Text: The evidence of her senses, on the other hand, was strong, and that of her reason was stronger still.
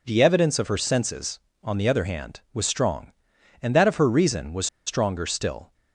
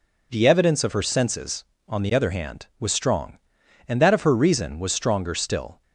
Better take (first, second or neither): second